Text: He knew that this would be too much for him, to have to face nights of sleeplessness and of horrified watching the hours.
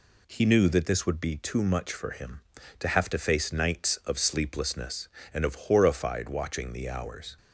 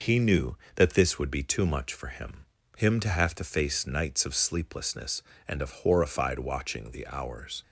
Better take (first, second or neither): first